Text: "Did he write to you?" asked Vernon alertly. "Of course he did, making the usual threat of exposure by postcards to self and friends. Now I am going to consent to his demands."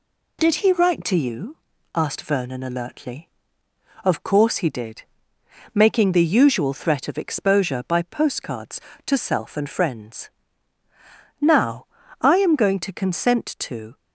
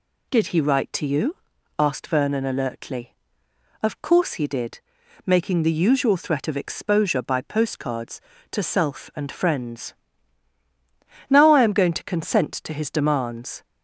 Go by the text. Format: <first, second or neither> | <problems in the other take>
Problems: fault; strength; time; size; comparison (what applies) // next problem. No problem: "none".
second | pauses between "Now" and "I"; at 11.8 s; 0.38 s long // stops before "his demands"; at 13.9 s